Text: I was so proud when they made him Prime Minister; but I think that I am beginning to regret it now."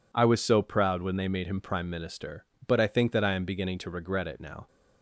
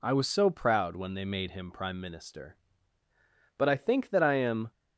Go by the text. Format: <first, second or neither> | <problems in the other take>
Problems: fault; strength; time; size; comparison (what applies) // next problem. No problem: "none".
first | stops before "beginning to regret it now"; at 4.7 s